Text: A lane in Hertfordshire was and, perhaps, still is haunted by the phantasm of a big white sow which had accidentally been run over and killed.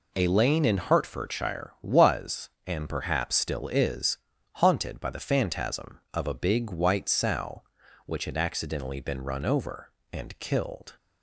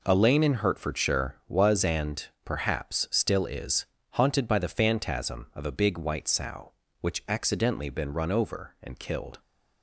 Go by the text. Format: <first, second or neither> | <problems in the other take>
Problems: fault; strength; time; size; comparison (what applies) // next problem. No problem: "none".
first | pauses between "is" and "haunted"; slight; at 3.8 s; 0.30 s long; also in the first // skips "had"; at 7.2 s